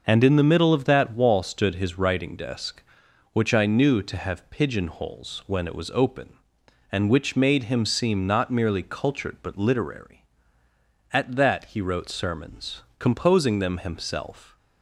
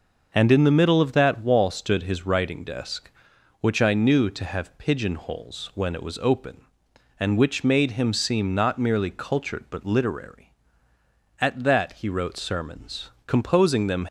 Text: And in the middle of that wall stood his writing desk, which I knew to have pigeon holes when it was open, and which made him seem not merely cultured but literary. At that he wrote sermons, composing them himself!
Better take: first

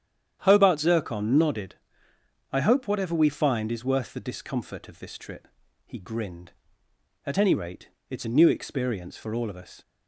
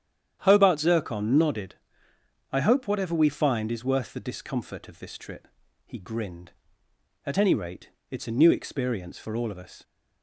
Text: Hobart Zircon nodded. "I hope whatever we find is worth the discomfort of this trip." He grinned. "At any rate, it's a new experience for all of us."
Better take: neither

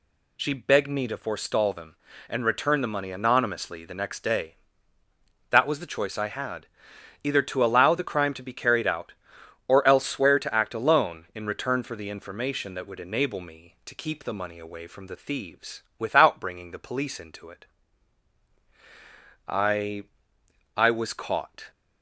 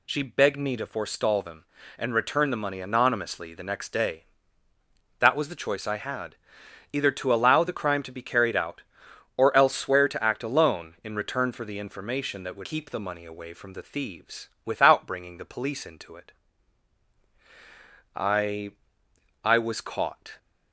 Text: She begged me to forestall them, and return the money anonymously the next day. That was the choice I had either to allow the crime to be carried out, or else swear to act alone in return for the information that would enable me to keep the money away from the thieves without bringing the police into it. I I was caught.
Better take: first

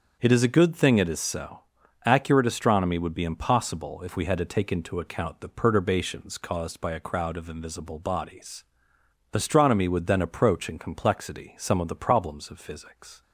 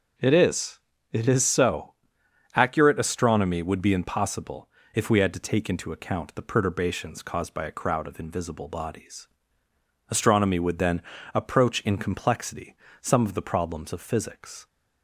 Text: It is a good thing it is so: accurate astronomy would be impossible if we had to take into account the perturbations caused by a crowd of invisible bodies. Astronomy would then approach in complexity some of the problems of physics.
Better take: first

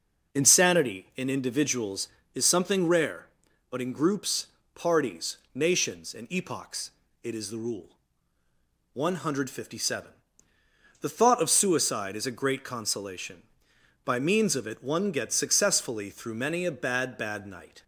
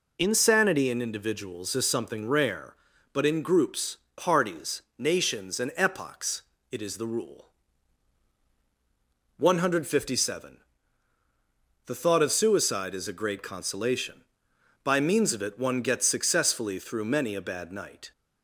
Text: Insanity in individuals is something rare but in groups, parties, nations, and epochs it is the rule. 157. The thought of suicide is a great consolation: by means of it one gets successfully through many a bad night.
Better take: second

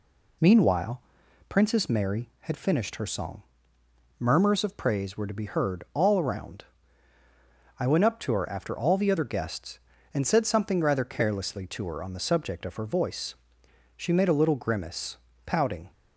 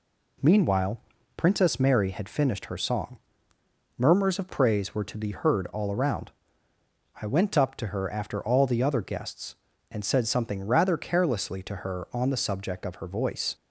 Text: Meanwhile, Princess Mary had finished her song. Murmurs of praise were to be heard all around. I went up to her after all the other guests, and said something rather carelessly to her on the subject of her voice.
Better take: second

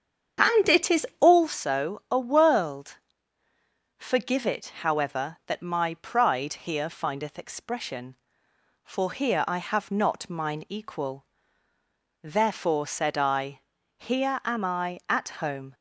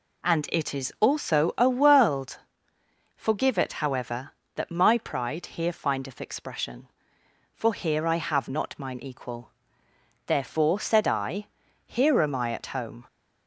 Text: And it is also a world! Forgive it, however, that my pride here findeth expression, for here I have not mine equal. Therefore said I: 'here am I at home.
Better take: second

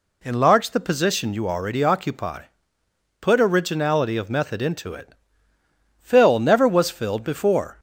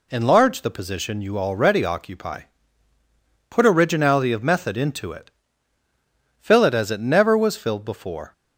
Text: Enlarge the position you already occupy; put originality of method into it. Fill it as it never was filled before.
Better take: second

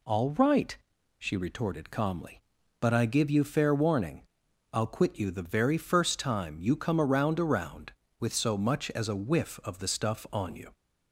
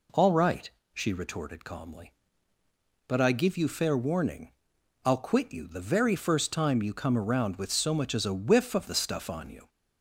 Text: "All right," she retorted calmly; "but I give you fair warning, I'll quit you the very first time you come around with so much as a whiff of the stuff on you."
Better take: second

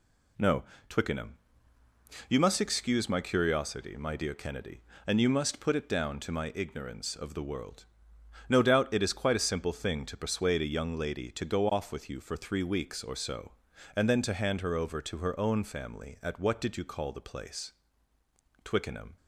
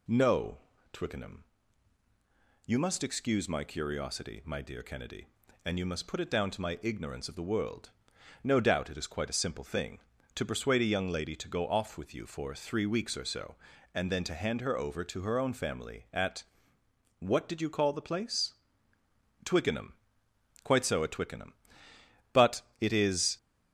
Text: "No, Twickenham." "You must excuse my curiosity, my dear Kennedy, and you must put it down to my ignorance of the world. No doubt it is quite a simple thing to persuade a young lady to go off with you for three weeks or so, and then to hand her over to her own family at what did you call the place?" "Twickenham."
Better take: first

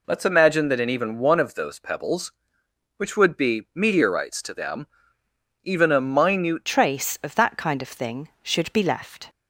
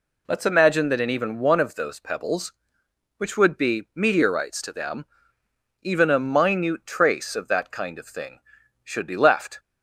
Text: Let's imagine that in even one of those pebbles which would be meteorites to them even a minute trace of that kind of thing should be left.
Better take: second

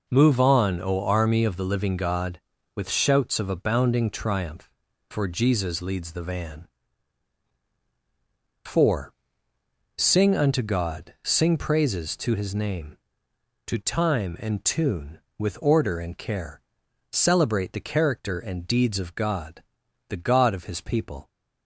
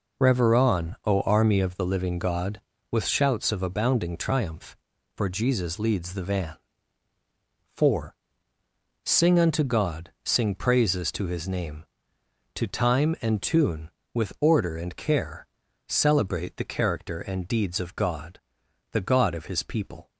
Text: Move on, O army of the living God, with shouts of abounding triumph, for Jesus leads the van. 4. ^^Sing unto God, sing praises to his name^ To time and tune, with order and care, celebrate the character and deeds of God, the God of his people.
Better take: first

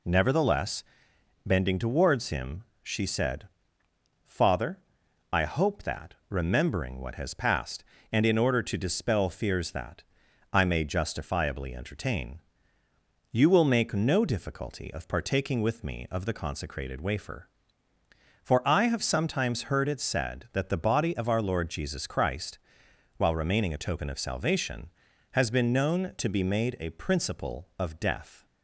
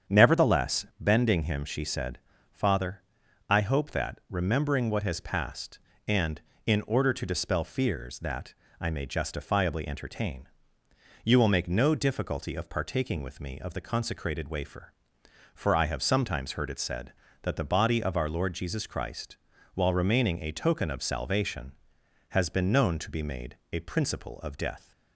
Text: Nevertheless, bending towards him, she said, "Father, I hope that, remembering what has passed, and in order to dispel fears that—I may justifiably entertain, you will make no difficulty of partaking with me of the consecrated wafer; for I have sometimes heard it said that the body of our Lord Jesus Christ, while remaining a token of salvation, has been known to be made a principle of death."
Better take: first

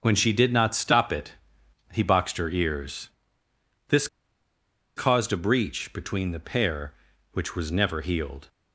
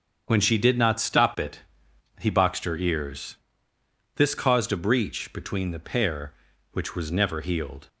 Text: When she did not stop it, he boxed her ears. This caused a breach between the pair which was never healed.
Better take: second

